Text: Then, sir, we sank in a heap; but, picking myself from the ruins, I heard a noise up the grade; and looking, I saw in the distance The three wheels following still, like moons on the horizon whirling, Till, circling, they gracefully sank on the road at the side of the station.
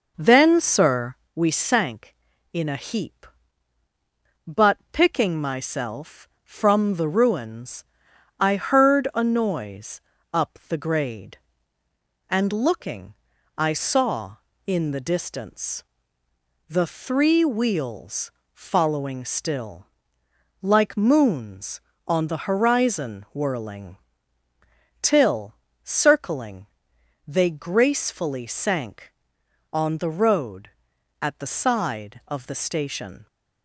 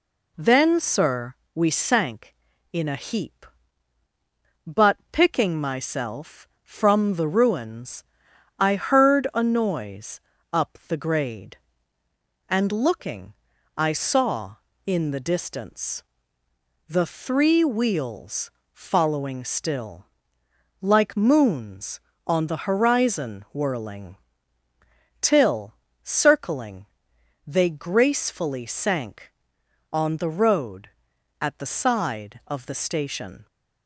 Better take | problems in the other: second | starts louder than the rest; noticeable; until 1.3 s; 5.5 dB // pauses between "noise" and "up"; slight; at 10.0 s; 0.32 s long; slight in the second // pauses between "distance" and "The"; noticeable; at 15.8 s; 0.86 s long; noticeable in the second // pauses between "wheels" and "following"; slight; at 18.3 s; 0.22 s long; slight in the second

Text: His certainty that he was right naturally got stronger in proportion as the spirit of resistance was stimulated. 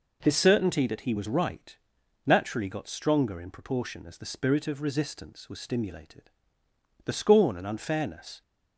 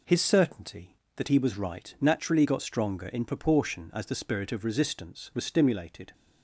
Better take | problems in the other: second | pauses between "right" and "naturally"; noticeable; at 1.7 s; 0.48 s long // goes on to say "The scorn and unfairness"; from 7.0 s on; 1.3 s long

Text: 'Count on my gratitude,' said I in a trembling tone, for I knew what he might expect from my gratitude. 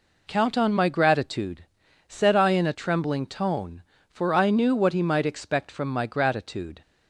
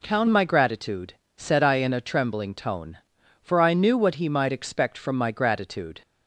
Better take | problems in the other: first | skips "on"; at 0.2 s

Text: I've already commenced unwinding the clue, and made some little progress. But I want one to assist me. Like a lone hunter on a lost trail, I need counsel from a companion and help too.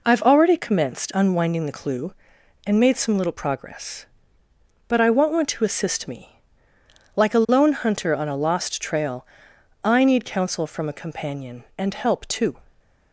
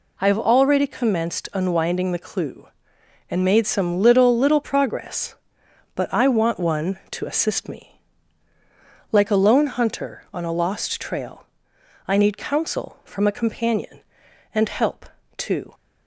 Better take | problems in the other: first | says "little" twice; at 4.3 s // pauses between "help" and "too"; slight; at 15.0 s; 0.30 s long

